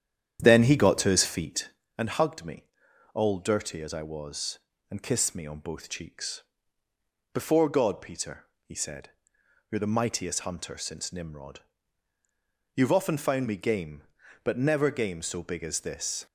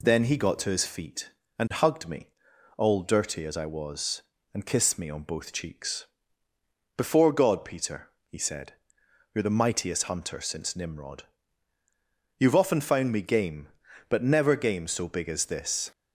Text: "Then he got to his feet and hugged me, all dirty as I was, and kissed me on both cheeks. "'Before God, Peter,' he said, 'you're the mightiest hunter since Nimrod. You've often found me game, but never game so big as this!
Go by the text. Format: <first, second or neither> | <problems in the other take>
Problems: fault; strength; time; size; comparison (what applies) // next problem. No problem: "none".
second | starts louder than the rest; strong; until 1.9 s; 9.5 dB